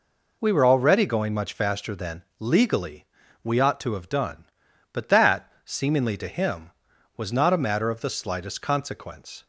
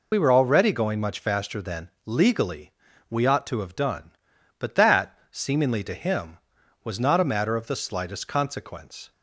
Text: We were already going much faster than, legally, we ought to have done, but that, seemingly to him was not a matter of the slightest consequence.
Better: first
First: none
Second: loses the start of "We"; at 0.1 s; 55 ms

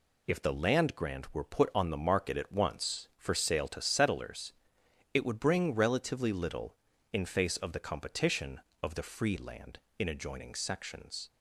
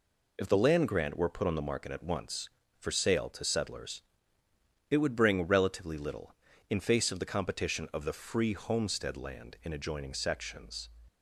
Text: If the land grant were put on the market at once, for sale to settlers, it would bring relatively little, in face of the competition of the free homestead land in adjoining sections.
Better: second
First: skips "homestead"; at 9.3 s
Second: none

